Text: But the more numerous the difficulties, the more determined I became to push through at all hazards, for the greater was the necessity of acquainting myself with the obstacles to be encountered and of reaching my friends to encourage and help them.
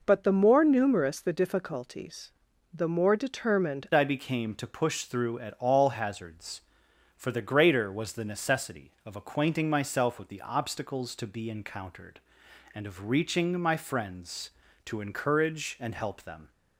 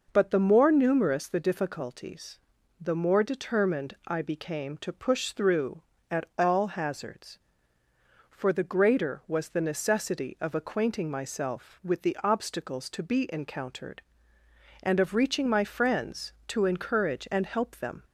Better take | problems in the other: second | changes voice at "I"; from 3.9 s on; 12.6 s long

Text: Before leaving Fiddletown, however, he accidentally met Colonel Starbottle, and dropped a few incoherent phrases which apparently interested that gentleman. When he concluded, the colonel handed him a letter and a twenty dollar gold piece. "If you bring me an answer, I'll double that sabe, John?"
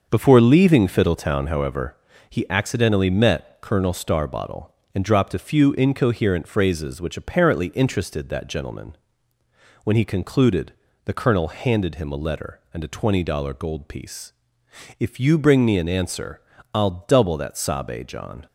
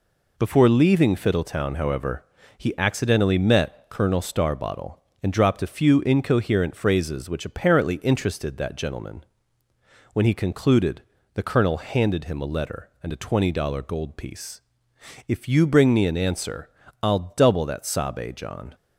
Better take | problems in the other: second | starts louder than the rest; until 1.6 s; 6.5 dB

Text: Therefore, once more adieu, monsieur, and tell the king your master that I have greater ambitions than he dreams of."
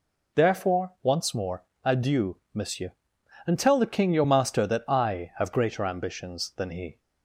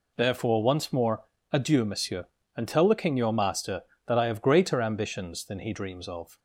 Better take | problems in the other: second | pauses between "more" and "adieu"; slight; at 1.6 s; 0.18 s long; slight in the second // stops before "dreams of"; at 6.9 s

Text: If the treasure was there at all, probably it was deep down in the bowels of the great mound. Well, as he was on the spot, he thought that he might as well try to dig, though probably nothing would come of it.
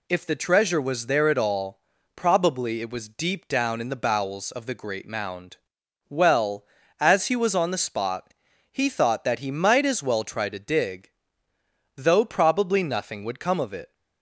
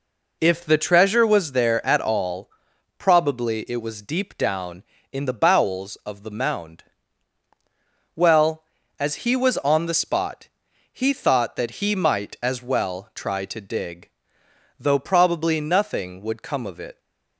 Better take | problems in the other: first | skips "great"; at 6.3 s

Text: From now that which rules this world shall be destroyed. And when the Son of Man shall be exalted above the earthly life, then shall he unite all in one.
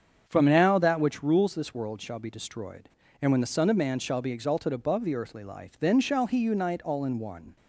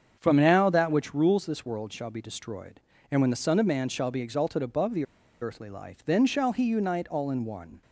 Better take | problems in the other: first | starts louder than the rest; strong; until 1.2 s; 7.5 dB; strong in the first // pauses between "the" and "earthly"; at 5.0 s; 0.36 s long

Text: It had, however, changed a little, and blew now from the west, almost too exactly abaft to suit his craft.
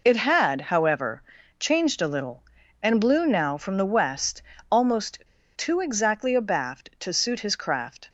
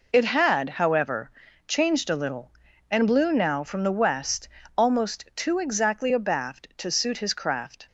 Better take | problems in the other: second | pauses between "almost" and "too"; slight; at 5.1 s; 0.35 s long

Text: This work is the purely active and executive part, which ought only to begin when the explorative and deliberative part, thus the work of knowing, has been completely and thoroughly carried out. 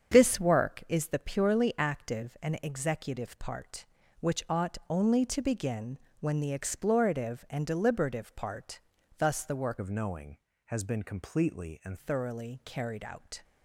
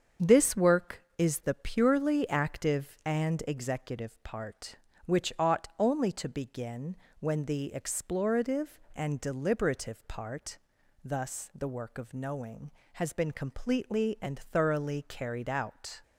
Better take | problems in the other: second | starts louder than the rest; strong; until 1.1 s; 7.5 dB; strong in the second // pauses between "begin" and "when"; slight; at 5.9 s; 0.24 s long; slight in the second // changes voice from "of" to "and"; from 9.8 to 11.9 s; 2.1 s long

